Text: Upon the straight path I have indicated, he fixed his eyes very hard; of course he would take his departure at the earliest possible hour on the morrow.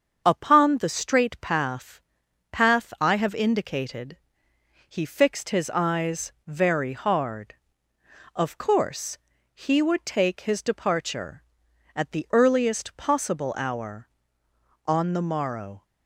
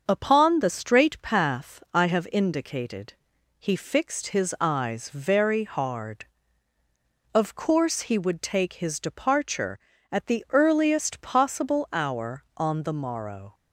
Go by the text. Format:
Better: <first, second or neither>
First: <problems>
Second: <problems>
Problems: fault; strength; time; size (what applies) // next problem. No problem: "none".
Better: second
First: starts louder than the rest; until 1.2 s; 7 dB // says "path" twice; at 2.5 s // pauses between "course" and "he"; slight; at 9.1 s; 0.36 s long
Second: starts louder than the rest; until 1.0 s; 7 dB